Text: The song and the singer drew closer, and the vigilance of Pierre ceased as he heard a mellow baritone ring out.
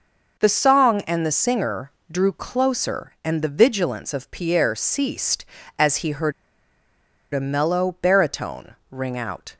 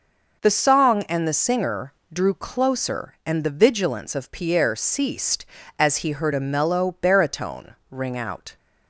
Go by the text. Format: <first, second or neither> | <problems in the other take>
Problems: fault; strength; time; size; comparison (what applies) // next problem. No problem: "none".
second | pauses between "singer" and "drew"; slight; at 1.9 s; 0.20 s long; slight in the second // pauses between "heard" and "a"; at 6.3 s; 1.0 s long // pauses between "baritone" and "ring"; slight; at 8.7 s; 0.16 s long; slight in the second